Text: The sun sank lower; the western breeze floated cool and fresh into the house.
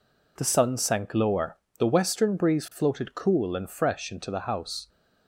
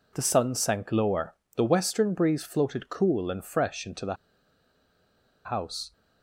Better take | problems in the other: first | pauses between "the" and "house"; strong; at 4.1 s; 1.3 s long

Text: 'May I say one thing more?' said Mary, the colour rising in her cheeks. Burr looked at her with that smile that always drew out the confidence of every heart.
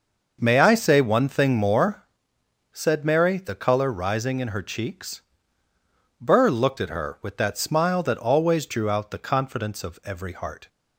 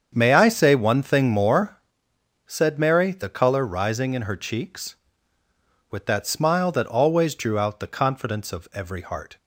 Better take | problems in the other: first | starts louder than the rest; strong; until 1.1 s; 7.5 dB; noticeable in the first // skips "Burr looked at her"; at 5.4 s

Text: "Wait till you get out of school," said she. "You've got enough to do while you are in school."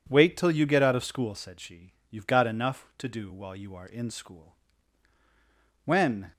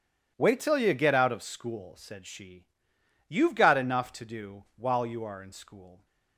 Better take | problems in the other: second | goes on to say "When"; slight; from 5.8 s on; 0.46 s long

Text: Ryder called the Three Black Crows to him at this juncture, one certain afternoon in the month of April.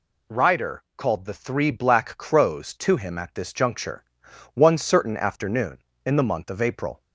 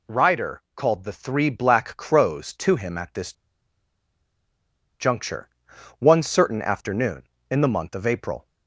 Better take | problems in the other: first | pauses between "this" and "juncture"; strong; at 3.3 s; 1.6 s long

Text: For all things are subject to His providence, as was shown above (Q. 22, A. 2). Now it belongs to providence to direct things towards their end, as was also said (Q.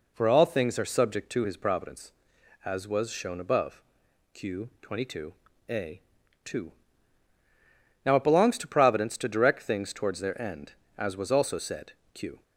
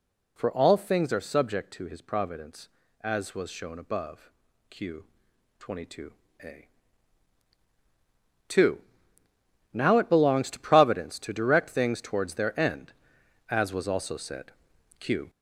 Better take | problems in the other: first | gets louder; noticeable; throughout; 4.5 dB

